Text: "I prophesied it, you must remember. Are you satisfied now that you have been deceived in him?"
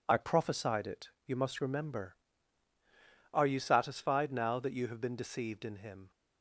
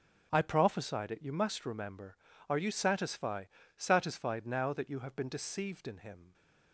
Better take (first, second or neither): first